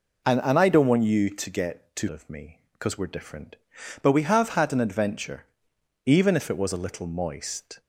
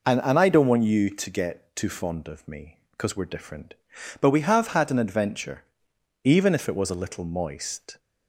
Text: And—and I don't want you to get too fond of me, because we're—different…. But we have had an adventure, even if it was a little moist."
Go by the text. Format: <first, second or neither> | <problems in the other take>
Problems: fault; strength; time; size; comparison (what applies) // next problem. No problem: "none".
second | skips "fond"; at 2.0 s